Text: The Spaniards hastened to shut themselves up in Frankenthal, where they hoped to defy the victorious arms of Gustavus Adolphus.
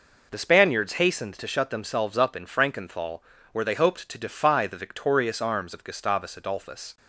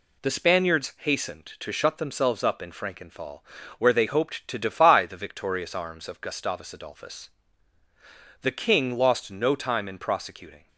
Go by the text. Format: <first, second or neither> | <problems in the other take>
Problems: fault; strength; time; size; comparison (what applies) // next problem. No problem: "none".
first | goes on to say "The king lost no time in prosecuting"; strong; from 8.4 s on; 2.2 s long